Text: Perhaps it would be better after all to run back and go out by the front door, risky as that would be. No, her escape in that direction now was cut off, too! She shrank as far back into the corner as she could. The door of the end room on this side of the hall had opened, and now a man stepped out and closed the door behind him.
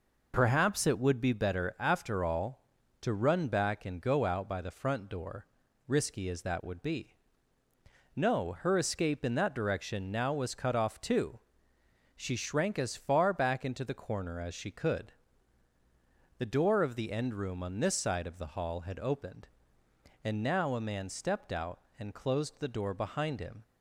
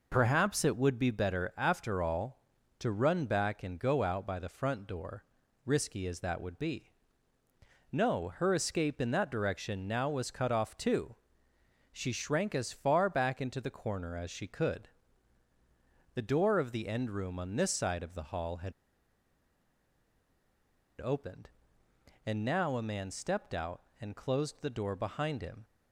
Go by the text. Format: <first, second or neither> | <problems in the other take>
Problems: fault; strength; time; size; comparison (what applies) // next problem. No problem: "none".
first | pauses between "had" and "opened"; strong; at 18.7 s; 2.2 s long